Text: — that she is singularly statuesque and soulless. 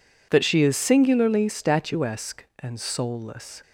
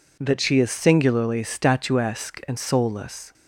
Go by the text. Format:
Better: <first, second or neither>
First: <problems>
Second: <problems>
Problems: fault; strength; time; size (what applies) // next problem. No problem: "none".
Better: neither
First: none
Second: none